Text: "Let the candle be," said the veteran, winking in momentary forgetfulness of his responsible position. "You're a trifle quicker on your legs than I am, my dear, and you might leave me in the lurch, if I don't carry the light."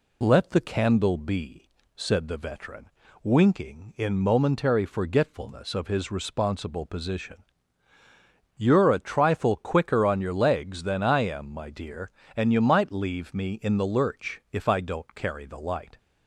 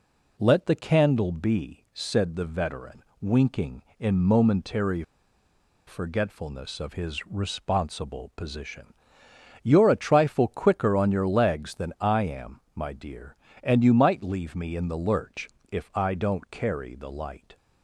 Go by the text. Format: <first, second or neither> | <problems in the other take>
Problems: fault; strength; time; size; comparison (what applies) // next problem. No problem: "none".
first | pauses between "momentary" and "forgetfulness"; noticeable; at 5.0 s; 0.84 s long